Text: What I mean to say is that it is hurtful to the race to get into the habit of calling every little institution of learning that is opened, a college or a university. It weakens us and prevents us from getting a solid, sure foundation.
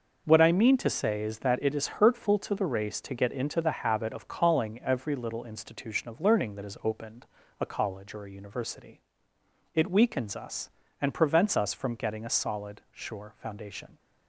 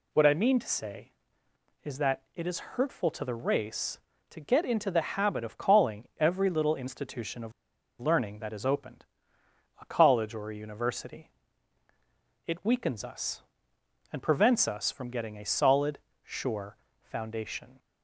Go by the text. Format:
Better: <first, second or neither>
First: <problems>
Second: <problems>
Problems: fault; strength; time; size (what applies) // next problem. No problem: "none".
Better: first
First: none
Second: pauses between "of" and "learning"; noticeable; at 7.5 s; 0.48 s long // pauses between "sure" and "foundation"; slight; at 16.7 s; 0.26 s long